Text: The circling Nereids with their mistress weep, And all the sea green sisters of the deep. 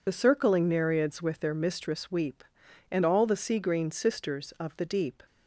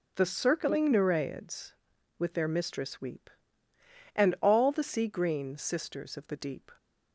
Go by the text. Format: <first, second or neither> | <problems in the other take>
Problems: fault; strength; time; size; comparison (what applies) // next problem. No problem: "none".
second | loses the start of "The"; at 0.0 s; 35 ms